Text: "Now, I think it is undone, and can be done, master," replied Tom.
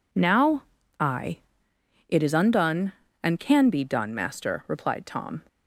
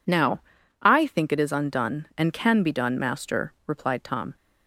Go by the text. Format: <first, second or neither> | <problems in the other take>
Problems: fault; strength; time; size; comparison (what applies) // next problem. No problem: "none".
second | skips "think"; at 1.7 s